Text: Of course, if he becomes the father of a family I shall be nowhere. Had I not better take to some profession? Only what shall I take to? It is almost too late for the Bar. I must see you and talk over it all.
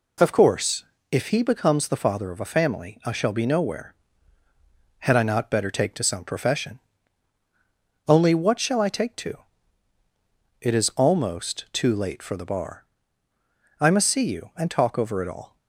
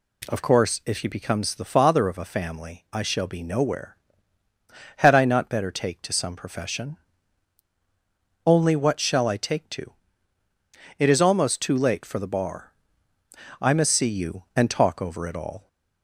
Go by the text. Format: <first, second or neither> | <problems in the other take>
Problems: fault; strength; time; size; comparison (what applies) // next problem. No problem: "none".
neither | none